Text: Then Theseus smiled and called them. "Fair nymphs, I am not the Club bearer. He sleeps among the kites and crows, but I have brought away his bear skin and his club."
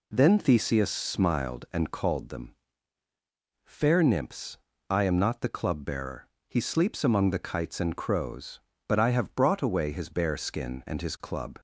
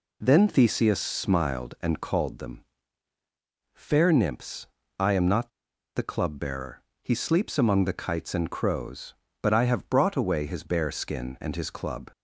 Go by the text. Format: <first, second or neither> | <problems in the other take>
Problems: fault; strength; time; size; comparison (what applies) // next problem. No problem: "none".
first | pauses between "not" and "the"; at 5.4 s; 0.45 s long